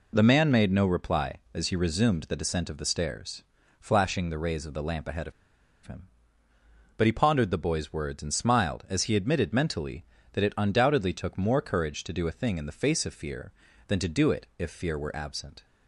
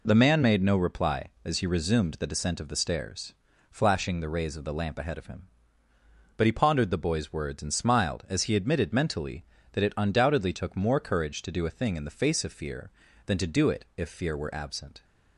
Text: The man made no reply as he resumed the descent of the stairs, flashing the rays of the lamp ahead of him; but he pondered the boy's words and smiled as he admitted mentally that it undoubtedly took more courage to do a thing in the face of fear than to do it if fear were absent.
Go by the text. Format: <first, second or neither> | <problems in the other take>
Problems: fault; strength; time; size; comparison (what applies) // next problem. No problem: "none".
second | pauses between "of" and "him"; noticeable; at 5.3 s; 0.52 s long